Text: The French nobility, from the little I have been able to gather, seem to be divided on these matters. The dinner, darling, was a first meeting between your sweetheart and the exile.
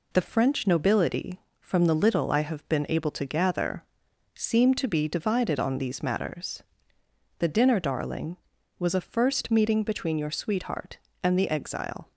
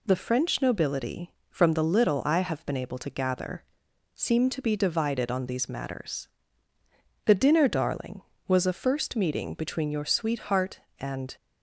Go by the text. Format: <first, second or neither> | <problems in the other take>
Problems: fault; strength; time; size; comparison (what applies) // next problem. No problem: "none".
first | stops before "the exile"; at 11.3 s